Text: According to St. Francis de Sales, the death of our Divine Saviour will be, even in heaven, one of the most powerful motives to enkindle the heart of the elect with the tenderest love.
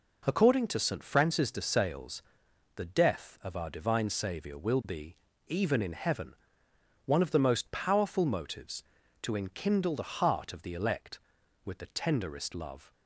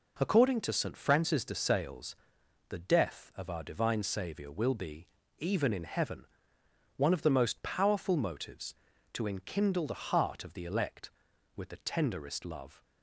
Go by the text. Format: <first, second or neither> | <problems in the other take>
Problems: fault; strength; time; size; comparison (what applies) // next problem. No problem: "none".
neither | none